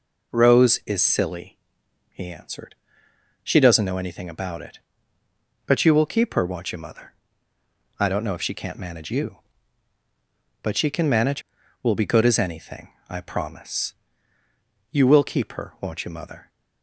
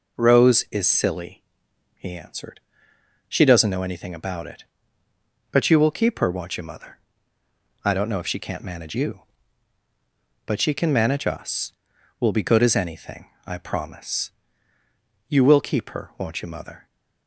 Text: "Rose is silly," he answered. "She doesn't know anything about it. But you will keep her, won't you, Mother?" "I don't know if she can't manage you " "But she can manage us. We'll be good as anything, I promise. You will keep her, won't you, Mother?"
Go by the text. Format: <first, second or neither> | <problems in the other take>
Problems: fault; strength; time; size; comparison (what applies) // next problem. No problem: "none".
second | skips "us"; at 11.6 s